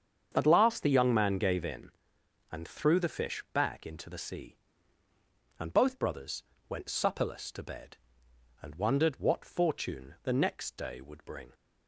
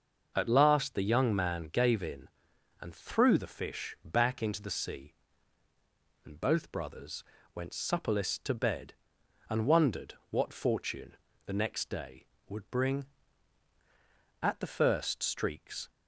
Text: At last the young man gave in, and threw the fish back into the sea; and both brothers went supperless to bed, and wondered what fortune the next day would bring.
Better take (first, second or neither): first